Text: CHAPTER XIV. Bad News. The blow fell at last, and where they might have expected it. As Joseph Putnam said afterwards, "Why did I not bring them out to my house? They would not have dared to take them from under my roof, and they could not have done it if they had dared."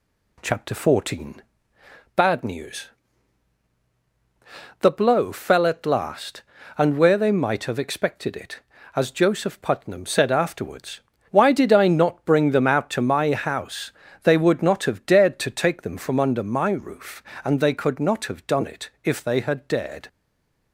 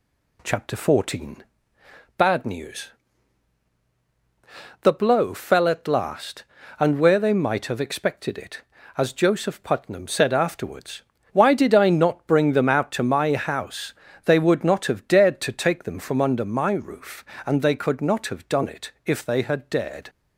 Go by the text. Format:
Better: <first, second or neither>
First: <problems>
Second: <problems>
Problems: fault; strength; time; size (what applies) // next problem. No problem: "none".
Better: second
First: stays silent after the last word; slight; from 20.0 s on; 0.7 s long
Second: none